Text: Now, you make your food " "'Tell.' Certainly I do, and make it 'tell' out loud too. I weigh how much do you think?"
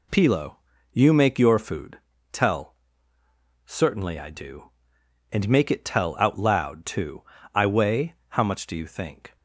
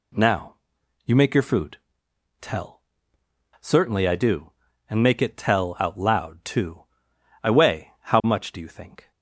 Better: second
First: says "Pilo" for "Now"; at 0.1 s // pauses between "weigh" and "how"; slight; at 8.1 s; 0.16 s long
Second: none

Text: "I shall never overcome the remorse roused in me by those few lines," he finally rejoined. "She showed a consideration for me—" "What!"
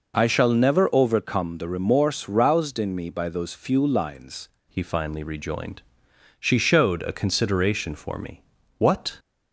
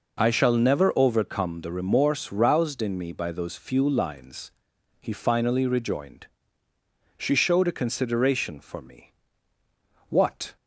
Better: second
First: changes voice at "he"; from 4.6 s on; 4.5 s long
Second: none

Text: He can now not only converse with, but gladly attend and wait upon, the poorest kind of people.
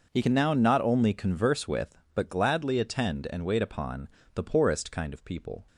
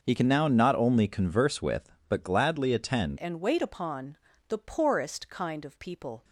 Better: first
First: none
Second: starts louder than the rest; until 1.0 s; 6.5 dB // changes voice at "and"; from 3.1 s on; 3.1 s long

